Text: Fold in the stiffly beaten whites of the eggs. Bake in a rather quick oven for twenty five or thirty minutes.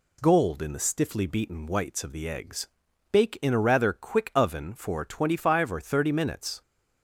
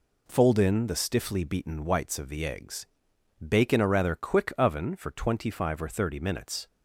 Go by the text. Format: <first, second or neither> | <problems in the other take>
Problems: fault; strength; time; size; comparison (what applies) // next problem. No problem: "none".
second | says "Gold" for "Fold"; at 0.2 s